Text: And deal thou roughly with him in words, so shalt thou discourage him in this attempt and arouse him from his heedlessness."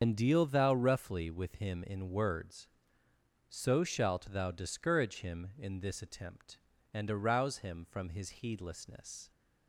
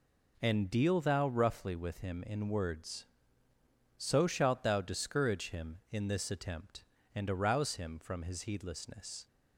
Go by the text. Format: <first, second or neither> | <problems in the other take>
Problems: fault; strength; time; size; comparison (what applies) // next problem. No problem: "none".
second | loses the start of "And"; at 0.0 s; 50 ms // starts louder than the rest; until 1.0 s; 7 dB